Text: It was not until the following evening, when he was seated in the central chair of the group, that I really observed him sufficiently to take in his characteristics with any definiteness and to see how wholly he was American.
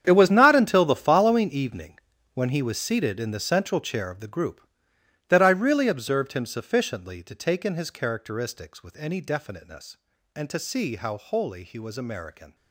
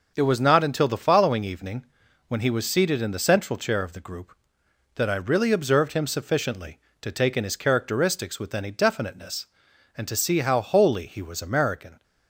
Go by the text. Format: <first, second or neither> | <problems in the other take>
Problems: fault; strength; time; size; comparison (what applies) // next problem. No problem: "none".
second | gets quieter; strong; throughout; 15 dB // starts louder than the rest; strong; until 1.0 s; 8.5 dB; also in the second